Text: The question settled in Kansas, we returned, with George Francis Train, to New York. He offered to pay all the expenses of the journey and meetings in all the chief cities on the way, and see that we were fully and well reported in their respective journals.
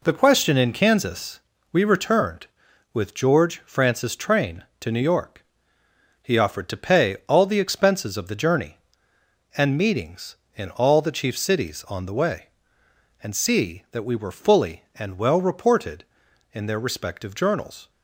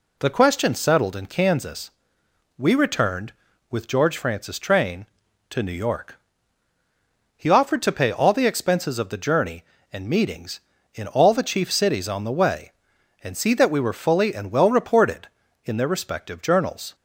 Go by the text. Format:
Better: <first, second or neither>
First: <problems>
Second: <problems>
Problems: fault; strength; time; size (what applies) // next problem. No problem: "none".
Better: second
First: skips "settled"; at 0.5 s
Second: none